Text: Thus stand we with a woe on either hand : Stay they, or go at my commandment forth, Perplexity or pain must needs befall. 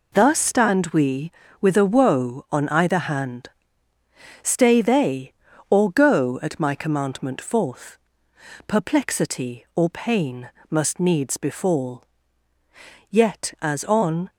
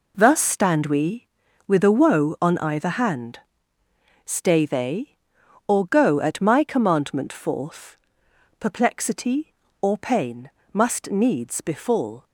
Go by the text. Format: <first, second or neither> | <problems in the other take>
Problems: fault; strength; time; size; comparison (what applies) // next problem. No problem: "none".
second | pauses between "pain" and "must"; slight; at 10.5 s; 0.18 s long; slight in the second // goes on to say "Yet as on"; noticeable; from 13.0 s on; 1.2 s long